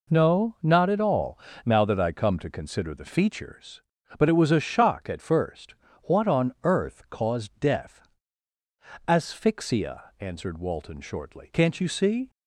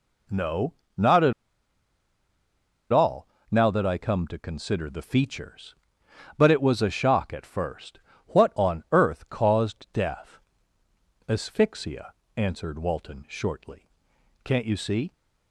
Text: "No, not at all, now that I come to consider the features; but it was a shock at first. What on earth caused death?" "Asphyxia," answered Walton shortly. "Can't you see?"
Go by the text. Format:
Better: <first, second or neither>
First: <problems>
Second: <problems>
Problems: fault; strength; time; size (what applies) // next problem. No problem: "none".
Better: first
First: none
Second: pauses between "at" and "all"; strong; at 1.3 s; 1.5 s long